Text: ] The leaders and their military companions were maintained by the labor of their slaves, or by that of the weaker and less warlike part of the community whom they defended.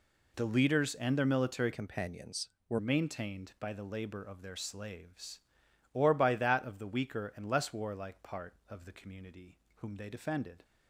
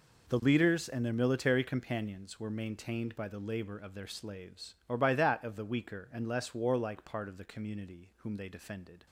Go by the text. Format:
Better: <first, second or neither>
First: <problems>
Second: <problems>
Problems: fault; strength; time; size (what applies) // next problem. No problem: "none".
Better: second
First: changes voice from "companions" to "were"; from 1.7 to 2.7 s; 1.0 s long // pauses between "community" and "whom"; slight; at 9.5 s; 0.22 s long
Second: none